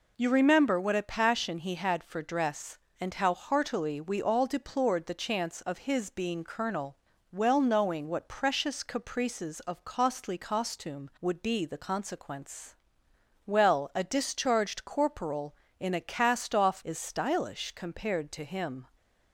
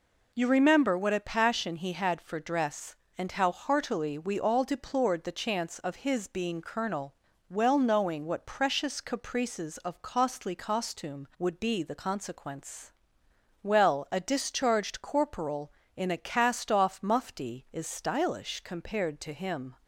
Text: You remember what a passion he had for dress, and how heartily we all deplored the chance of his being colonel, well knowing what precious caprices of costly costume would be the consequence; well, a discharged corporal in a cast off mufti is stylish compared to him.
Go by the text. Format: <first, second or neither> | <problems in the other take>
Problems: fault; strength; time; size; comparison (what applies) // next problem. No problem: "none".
second | skips "mufti"; at 16.8 s